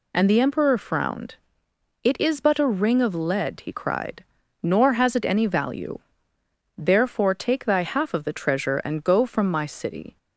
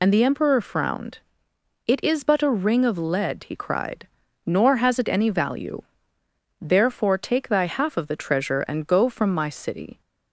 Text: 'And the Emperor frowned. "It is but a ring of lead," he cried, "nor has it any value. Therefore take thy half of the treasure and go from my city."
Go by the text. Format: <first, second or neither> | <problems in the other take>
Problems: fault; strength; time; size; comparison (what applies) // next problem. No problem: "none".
first | loses the start of "And"; at 0.0 s; 45 ms